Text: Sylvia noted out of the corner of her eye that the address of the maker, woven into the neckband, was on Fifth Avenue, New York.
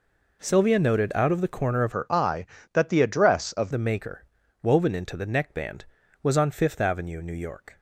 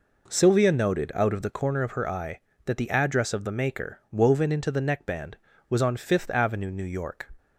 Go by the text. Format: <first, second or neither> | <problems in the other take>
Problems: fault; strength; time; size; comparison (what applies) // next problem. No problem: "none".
second | changes voice from "her" to "of"; from 1.9 to 3.7 s; 1.8 s long